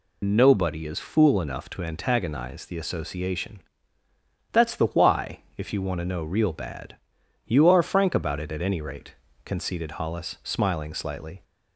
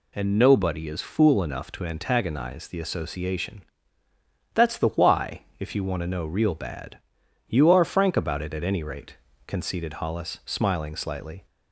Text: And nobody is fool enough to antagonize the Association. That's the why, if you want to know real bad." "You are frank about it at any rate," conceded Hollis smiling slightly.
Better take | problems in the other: second | loses the start of "And"; at 0.2 s; 95 ms

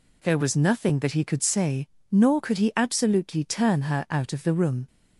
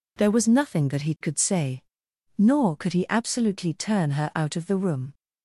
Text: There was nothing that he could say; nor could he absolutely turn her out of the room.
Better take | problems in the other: neither | none

